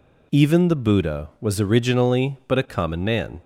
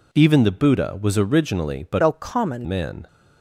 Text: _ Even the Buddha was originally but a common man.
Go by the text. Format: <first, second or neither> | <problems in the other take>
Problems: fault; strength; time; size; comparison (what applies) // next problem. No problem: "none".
first | changes voice from "a" to "common"; from 2.0 to 2.6 s; 0.6 s long